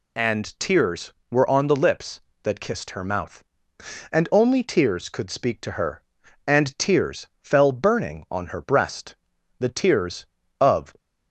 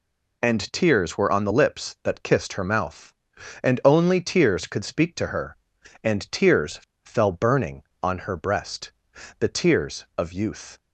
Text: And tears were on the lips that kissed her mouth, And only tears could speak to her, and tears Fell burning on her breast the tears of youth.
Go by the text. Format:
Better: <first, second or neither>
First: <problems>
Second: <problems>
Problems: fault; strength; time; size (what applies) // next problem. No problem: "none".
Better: second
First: pauses between "tears" and "Fell"; slight; at 7.2 s; 0.16 s long // pauses between "breast" and "the"; noticeable; at 9.1 s; 0.46 s long // stops before "youth"; at 10.9 s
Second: pauses between "tears" and "Fell"; slight; at 6.7 s; 0.24 s long // pauses between "breast" and "the"; noticeable; at 8.9 s; 0.48 s long